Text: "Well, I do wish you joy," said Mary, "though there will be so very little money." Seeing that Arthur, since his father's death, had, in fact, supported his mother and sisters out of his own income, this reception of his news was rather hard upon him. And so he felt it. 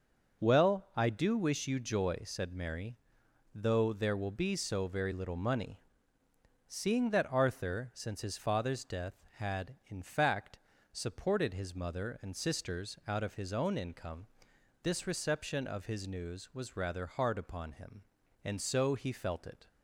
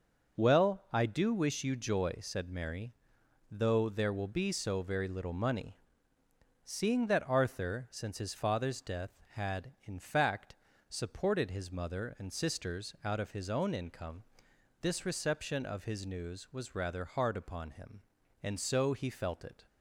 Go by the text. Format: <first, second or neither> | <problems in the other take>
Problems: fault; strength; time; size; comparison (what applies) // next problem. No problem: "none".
neither | starts louder than the rest; the same in both